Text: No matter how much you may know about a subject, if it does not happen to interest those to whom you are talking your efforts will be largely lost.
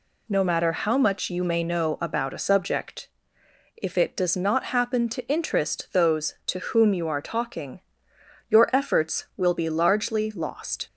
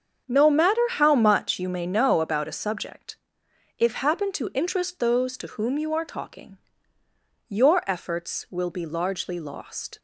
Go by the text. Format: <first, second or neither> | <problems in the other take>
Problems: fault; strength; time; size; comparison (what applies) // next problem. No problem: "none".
first | starts louder than the rest; strong; until 1.3 s; 7.5 dB // skips "it does not"; at 3.9 s // pauses between "talking" and "your"; noticeable; at 6.5 s; 0.90 s long; noticeable in the first